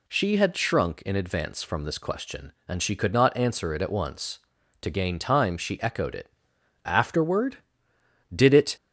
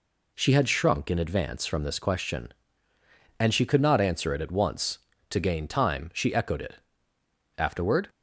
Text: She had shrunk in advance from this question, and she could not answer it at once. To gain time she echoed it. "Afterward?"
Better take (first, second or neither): second